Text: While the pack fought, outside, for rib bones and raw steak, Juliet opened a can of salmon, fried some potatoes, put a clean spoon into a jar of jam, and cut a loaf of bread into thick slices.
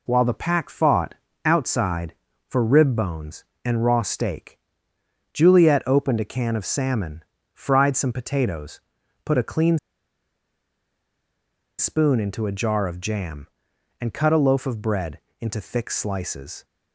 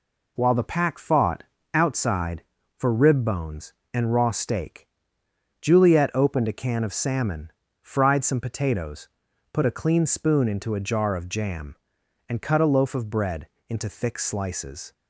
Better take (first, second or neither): second